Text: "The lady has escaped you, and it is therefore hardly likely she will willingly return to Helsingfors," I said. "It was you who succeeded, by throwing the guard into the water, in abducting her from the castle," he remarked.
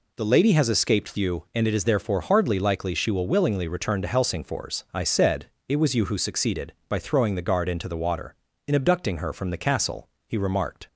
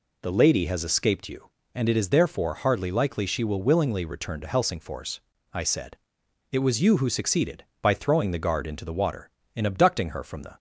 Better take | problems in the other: first | stops before "castle he remarked"; at 10.5 s

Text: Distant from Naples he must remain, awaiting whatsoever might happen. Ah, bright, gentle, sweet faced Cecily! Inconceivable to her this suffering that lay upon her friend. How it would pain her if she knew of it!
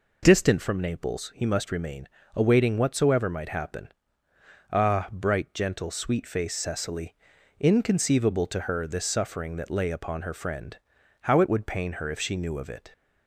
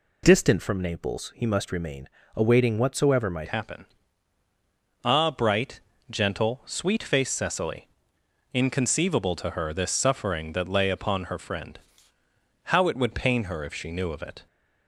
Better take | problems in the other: first | changes voice at "happen"; from 3.4 s on; 11.0 s long

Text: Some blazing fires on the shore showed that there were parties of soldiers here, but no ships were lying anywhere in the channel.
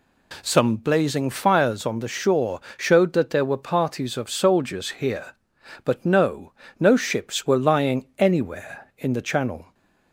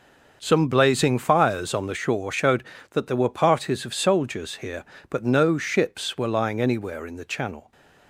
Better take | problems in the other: second | pauses between "shore" and "showed"; slight; at 2.5 s; 0.18 s long // says "no" twice; at 6.7 s

